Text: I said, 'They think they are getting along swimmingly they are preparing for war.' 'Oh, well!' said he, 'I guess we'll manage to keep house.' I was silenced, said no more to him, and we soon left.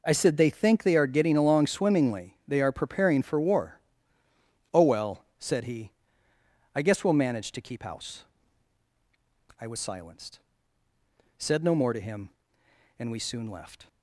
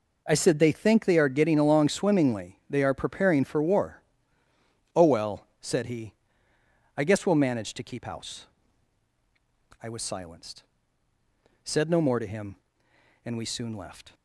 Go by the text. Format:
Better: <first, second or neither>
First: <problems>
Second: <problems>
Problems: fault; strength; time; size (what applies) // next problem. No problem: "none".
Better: neither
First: none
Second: none